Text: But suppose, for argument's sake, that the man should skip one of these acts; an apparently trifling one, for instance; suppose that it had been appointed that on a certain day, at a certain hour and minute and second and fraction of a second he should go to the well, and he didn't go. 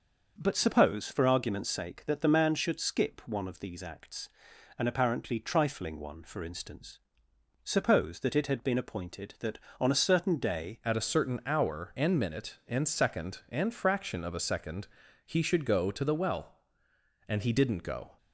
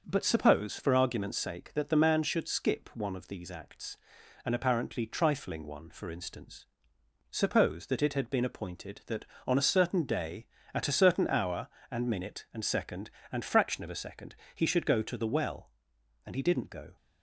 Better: second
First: starts louder than the rest; noticeable; until 1.3 s; 6 dB // changes voice at "at"; from 10.8 s on; 7.3 s long // pauses between "second" and "he"; slight; at 14.8 s; 0.36 s long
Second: starts louder than the rest; noticeable; until 1.0 s; 6 dB // pauses between "second" and "he"; slight; at 14.3 s; 0.18 s long

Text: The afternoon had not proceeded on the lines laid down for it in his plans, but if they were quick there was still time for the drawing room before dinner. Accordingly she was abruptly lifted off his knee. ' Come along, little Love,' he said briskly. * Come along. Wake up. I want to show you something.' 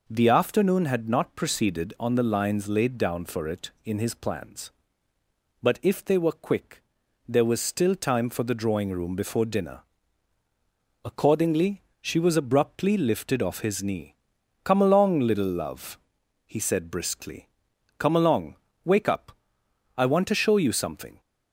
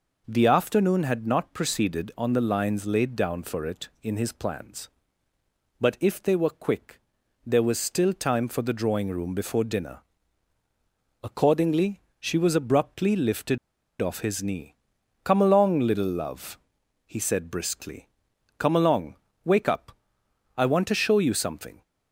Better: first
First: pauses between "quick" and "there"; noticeable; at 6.8 s; 0.46 s long // pauses between "Accordingly" and "she"; slight; at 11.8 s; 0.18 s long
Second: pauses between "quick" and "there"; noticeable; at 6.9 s; 0.46 s long // pauses between "Accordingly" and "she"; slight; at 12.0 s; 0.18 s long // pauses between "lifted" and "off"; at 13.5 s; 0.43 s long

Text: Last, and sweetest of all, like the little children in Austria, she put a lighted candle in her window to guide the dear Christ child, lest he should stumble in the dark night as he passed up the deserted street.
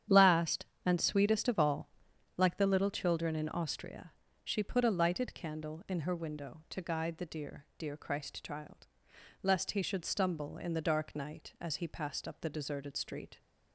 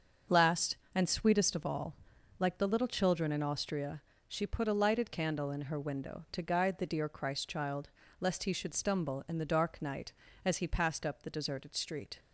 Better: second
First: starts louder than the rest; strong; until 1.3 s; 9.5 dB // says "dear" twice; at 7.7 s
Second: starts louder than the rest; until 1.4 s; 6.5 dB

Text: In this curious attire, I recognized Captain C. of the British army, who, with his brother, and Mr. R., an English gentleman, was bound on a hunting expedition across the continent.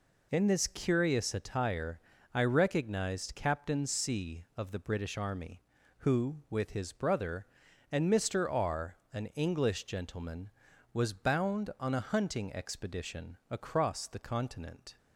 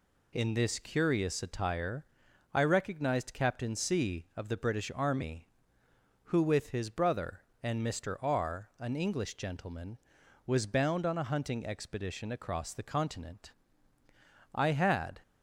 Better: first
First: none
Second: goes on to say "I had"; noticeable; from 14.5 s on; 0.68 s long

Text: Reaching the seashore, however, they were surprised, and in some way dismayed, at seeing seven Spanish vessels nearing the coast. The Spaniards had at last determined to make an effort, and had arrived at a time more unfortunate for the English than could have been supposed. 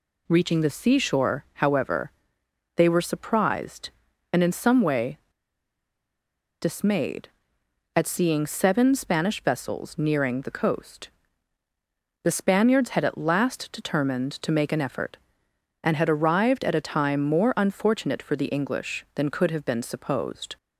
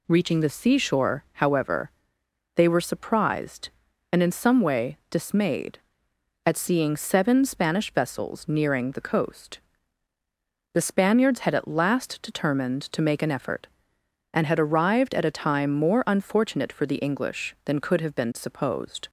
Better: second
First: pauses between "way" and "dismayed"; strong; at 5.1 s; 1.4 s long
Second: none

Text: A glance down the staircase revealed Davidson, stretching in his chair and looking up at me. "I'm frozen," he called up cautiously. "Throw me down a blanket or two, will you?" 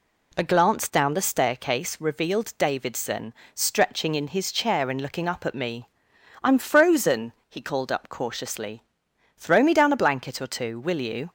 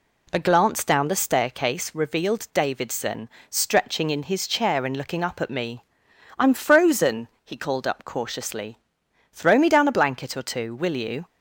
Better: neither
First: none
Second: none

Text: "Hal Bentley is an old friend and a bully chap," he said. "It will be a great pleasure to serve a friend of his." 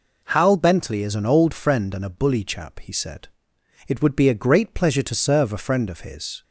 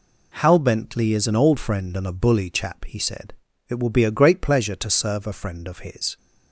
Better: second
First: says "would" for "will"; at 4.0 s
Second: none

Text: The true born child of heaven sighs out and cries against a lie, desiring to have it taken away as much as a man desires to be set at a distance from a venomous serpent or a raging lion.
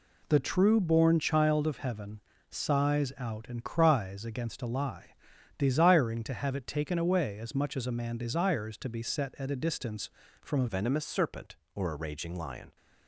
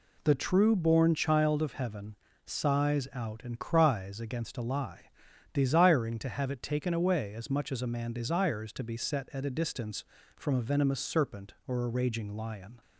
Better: second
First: pauses between "heaven" and "sighs"; slight; at 2.2 s; 0.26 s long // changes voice at "venomous"; from 10.6 s on; 2.1 s long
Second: pauses between "heaven" and "sighs"; slight; at 2.1 s; 0.26 s long

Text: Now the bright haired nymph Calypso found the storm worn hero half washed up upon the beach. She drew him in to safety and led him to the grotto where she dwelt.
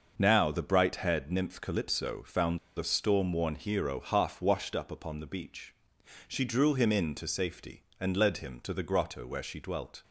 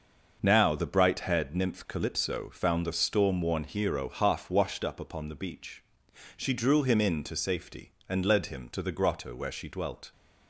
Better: second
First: starts louder than the rest; noticeable; until 1.1 s; 6 dB // pauses between "found" and "the"; slight; at 2.5 s; 0.18 s long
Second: starts louder than the rest; noticeable; until 1.4 s; 6 dB

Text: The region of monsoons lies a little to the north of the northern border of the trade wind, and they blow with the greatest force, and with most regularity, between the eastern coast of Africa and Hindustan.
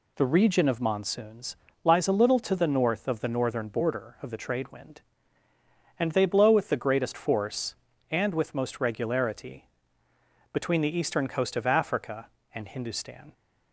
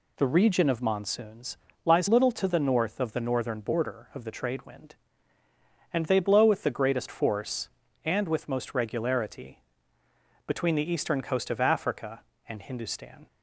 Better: first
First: pauses between "monsoons" and "lies"; slight; at 1.5 s; 0.28 s long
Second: pauses between "monsoons" and "lies"; slight; at 1.5 s; 0.28 s long // skips "a"; at 2.0 s

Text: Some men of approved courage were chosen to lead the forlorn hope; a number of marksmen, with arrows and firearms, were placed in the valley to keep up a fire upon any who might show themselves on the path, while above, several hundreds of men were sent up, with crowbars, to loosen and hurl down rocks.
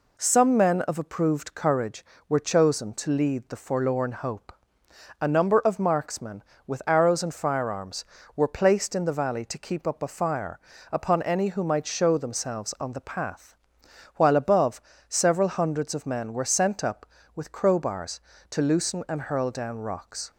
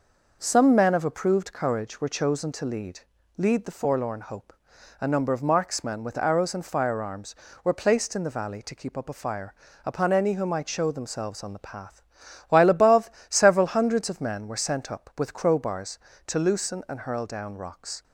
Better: first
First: pauses between "fire" and "upon"; slight; at 10.5 s; 0.32 s long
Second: says "lead" twice; at 3.3 s // pauses between "fire" and "upon"; slight; at 9.5 s; 0.32 s long

